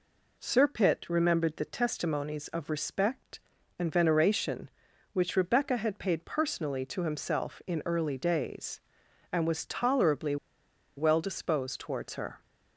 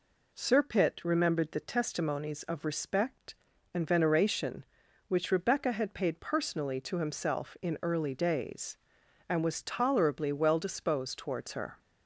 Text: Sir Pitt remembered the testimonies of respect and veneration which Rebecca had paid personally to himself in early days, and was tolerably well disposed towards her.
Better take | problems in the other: second | pauses between "tolerably" and "well"; noticeable; at 10.3 s; 0.61 s long

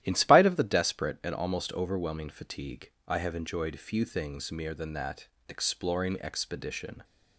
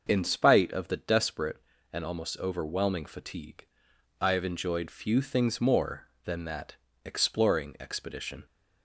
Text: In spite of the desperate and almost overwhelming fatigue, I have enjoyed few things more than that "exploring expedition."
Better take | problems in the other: second | starts louder than the rest; strong; until 1.0 s; 13 dB; noticeable in the second // says "mere" for "more"; at 4.5 s // pauses between "that" and "exploring"; slight; at 5.2 s; 0.20 s long; slight in the second

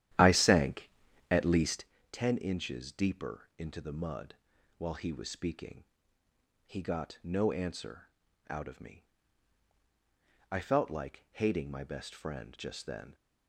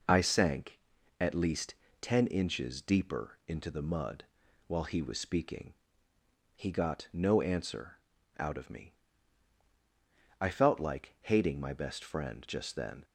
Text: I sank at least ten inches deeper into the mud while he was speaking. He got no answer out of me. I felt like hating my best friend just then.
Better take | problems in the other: second | starts louder than the rest; strong; until 1.9 s; 11.5 dB // pauses between "least" and "ten"; slight; at 1.8 s; 0.24 s long; slight in the second // pauses between "mud" and "while"; at 4.3 s; 0.42 s long; also in the second // pauses between "answer" and "out"; at 8.0 s; 0.40 s long; also in the second

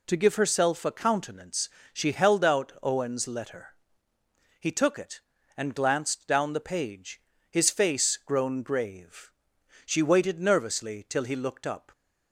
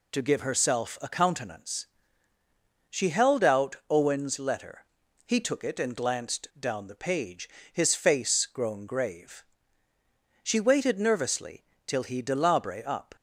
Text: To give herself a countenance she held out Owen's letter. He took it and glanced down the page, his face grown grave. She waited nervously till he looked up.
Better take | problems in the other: first | pauses between "countenance" and "she"; at 1.8 s; 1.0 s long; slight in the first // pauses between "nervously" and "till"; slight; at 11.6 s; 0.22 s long // says "delabre" for "looked"; at 12.2 s

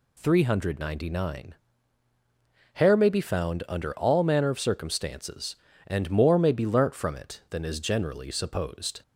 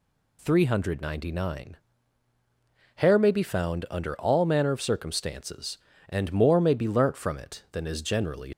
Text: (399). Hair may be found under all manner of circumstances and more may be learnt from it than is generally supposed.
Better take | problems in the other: first | stops before "supposed"; at 8.5 s

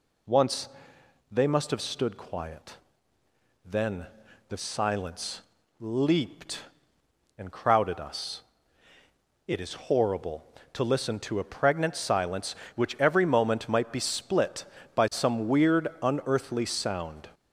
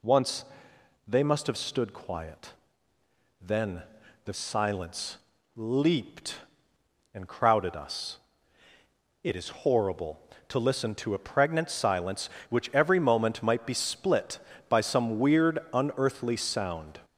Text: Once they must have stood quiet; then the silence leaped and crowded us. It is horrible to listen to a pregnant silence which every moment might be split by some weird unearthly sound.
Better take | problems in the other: neither | pauses between "Once" and "they"; noticeable; the same in both // pauses between "then" and "the"; the same in both // pauses between "silence" and "leaped"; the same in both

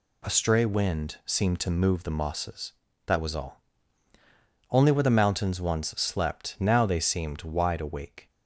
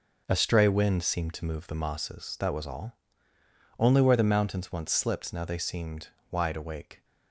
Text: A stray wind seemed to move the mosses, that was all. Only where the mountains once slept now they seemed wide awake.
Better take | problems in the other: first | says "slipped" for "slept"; at 4.9 s // pauses between "seemed" and "wide"; slight; at 6.0 s; 0.22 s long

